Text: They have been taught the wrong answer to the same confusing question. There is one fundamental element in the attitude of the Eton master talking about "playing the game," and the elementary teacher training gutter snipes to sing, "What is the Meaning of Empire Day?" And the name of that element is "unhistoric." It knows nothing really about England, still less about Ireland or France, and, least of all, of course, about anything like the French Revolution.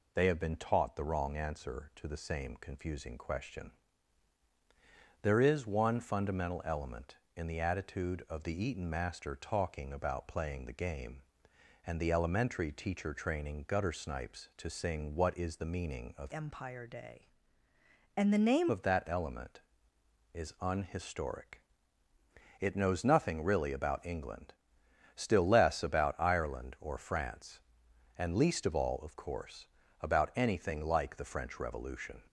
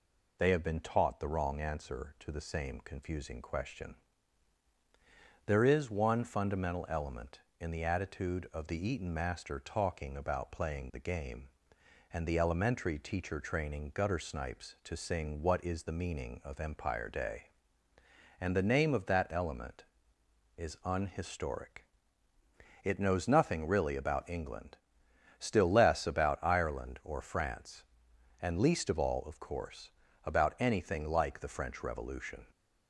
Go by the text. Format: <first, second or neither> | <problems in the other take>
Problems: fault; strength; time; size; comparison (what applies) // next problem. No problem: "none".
second | changes voice from "Empire" to "name"; from 16.3 to 18.6 s; 2.3 s long